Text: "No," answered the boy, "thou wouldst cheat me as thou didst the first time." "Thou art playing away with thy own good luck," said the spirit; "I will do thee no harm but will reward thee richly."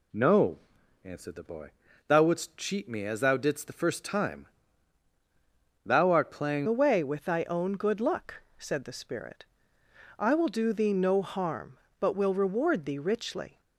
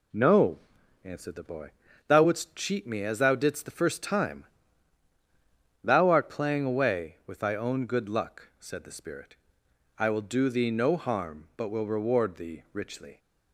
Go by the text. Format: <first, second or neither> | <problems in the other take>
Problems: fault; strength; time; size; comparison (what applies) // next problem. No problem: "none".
second | changes voice at "away"; from 6.6 s on; 6.9 s long